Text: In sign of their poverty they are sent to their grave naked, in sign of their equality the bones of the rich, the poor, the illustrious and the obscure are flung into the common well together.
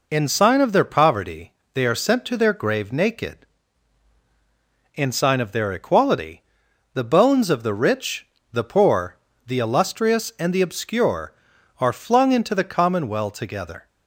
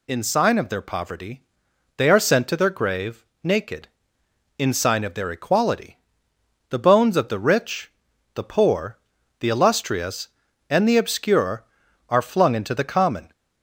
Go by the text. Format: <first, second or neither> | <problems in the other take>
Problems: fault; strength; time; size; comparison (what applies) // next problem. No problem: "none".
first | pauses between "poverty" and "they"; noticeable; at 1.4 s; 0.54 s long; slight in the first // pauses between "grave" and "naked"; slight; at 3.2 s; 0.20 s long // pauses between "equality" and "the"; noticeable; at 5.9 s; 0.70 s long; noticeable in the first // stops before "well together"; at 13.3 s